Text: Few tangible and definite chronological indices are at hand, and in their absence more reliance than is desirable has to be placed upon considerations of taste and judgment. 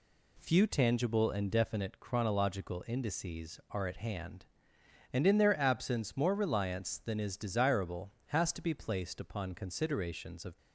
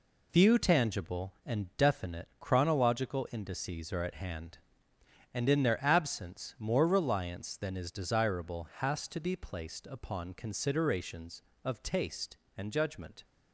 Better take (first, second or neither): second